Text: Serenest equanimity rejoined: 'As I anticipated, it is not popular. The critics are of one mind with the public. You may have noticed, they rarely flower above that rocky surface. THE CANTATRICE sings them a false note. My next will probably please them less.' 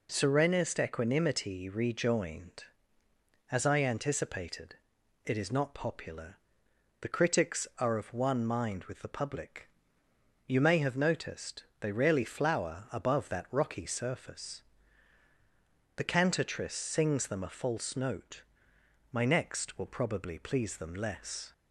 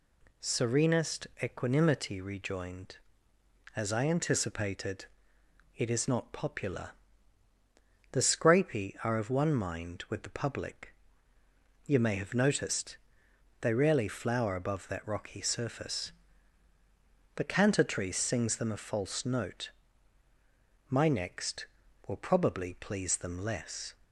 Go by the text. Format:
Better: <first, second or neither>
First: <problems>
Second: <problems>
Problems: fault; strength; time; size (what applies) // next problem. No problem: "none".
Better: first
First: none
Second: says "scrapy" for "critics"; at 8.2 s